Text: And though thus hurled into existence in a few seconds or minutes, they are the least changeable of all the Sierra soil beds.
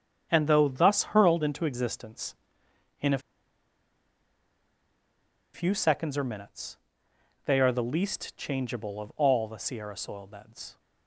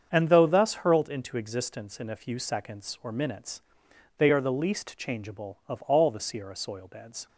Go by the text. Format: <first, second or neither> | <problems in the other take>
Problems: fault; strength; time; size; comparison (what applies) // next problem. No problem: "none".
second | starts louder than the rest; strong; until 1.3 s; 8 dB; strong in the second // pauses between "a" and "few"; strong; at 3.1 s; 2.3 s long